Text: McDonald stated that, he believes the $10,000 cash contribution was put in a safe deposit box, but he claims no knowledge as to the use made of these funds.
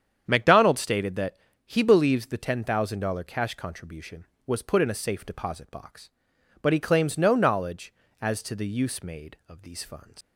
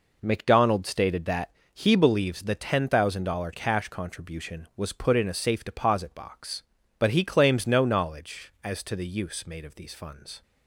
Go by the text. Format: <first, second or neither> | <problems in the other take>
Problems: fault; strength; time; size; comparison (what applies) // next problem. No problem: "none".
second | starts louder than the rest; strong; until 1.2 s; 8.5 dB // leaves "funds" unfinished; at 10.2 s; 120 ms